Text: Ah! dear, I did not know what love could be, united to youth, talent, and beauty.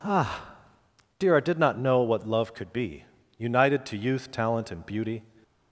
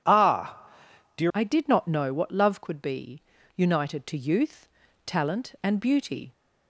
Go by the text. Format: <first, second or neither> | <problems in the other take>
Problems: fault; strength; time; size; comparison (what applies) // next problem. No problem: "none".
first | changes voice at "I"; from 1.3 s on; 5.0 s long